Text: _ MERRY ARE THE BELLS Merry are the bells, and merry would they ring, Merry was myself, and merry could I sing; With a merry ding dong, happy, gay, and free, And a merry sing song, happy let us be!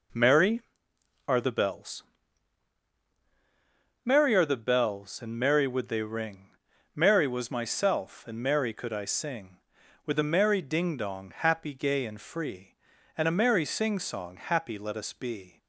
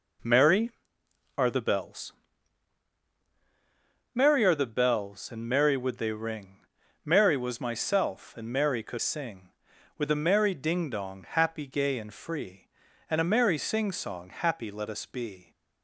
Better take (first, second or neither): first